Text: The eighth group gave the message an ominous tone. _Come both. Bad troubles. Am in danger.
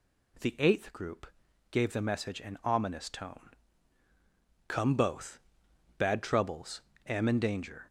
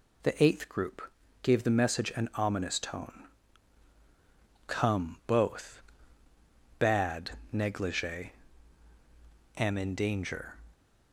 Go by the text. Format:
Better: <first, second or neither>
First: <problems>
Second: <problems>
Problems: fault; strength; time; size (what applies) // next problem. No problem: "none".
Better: first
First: pauses between "group" and "gave"; at 1.2 s; 0.44 s long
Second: pauses between "group" and "gave"; at 1.0 s; 0.42 s long // says "negligee" for "troubles"; at 7.5 s